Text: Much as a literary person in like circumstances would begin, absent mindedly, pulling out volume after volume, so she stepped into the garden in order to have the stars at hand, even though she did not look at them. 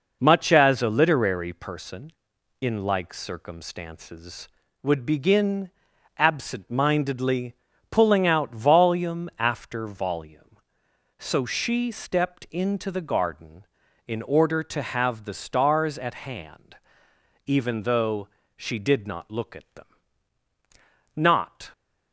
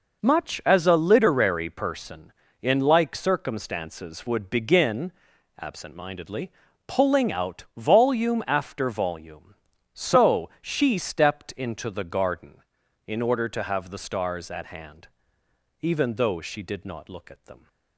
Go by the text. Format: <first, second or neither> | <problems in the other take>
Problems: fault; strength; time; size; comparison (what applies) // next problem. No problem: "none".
second | pauses between "though" and "she"; slight; at 18.2 s; 0.30 s long // goes on to say "Not"; from 21.1 s on; 0.56 s long